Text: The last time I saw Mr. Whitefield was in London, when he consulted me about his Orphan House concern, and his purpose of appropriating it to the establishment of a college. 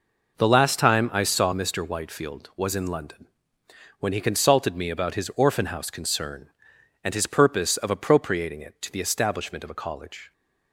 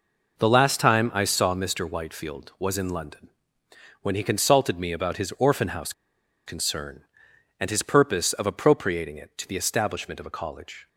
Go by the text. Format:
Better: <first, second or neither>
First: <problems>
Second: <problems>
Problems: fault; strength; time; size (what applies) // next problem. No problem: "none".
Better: first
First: none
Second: pauses between "House" and "concern"; noticeable; at 5.9 s; 0.52 s long